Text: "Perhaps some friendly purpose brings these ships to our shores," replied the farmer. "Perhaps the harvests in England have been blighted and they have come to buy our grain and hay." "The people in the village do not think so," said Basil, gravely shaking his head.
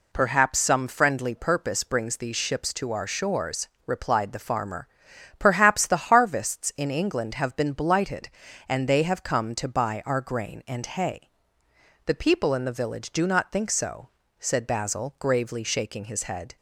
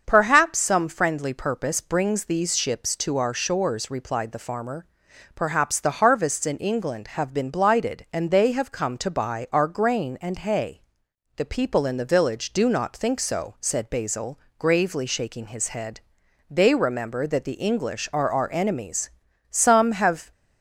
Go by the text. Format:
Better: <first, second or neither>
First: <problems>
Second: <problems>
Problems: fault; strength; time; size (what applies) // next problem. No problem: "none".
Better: first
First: none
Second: starts louder than the rest; until 1.0 s; 6.5 dB // goes on to say "They remember that the English are our enemies Some have"; strong; from 16.4 s on; 3.8 s long